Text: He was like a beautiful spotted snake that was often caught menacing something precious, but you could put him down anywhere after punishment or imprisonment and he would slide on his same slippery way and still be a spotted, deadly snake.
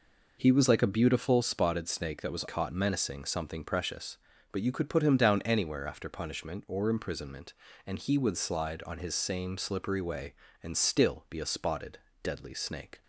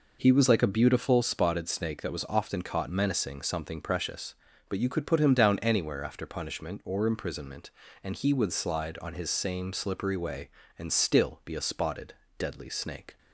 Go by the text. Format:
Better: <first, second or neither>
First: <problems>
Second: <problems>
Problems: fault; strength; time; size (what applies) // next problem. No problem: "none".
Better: second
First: skips "often"; at 2.4 s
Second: none